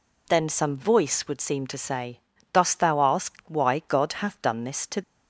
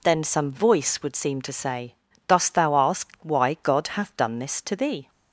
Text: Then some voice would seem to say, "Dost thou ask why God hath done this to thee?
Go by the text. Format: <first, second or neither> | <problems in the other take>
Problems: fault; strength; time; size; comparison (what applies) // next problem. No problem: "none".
second | stops before "thee"; at 5.0 s